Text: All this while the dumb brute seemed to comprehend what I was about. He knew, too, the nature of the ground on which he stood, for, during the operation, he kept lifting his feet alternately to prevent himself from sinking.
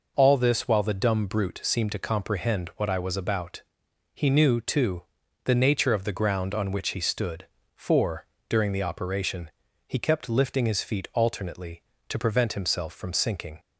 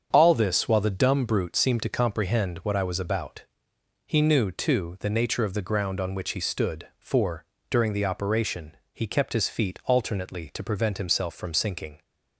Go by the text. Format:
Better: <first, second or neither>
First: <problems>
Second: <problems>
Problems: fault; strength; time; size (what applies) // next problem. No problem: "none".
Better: first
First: none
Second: starts louder than the rest; strong; until 1.1 s; 7.5 dB // skips "lifting"; at 9.3 s